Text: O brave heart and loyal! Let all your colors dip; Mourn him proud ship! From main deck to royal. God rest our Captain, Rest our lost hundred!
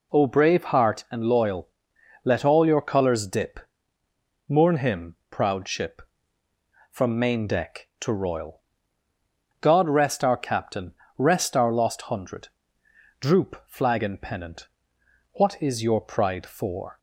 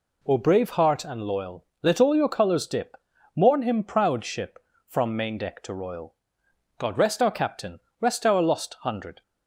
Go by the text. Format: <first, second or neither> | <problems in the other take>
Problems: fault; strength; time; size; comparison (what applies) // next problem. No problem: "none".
second | goes on to say "Droop flag and pennant What is your pride for"; strong; from 13.1 s on; 3.7 s long